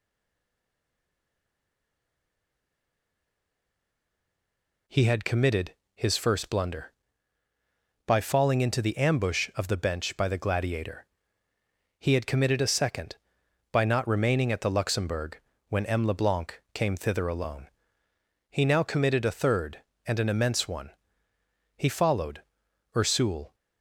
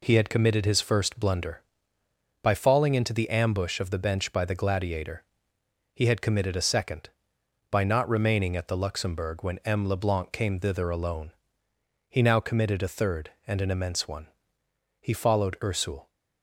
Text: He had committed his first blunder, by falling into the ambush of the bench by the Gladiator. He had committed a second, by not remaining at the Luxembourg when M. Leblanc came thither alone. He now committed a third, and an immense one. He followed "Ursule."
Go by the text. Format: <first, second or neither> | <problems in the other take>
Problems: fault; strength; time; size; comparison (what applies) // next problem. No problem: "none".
second | stays silent before the first word; strong; until 4.8 s; 4.8 s long // pauses between "committed" and "his"; slight; at 5.7 s; 0.20 s long // pauses between "Luxembourg" and "when"; slight; at 15.4 s; 0.28 s long // pauses between "followed" and "Ursule"; noticeable; at 22.4 s; 0.52 s long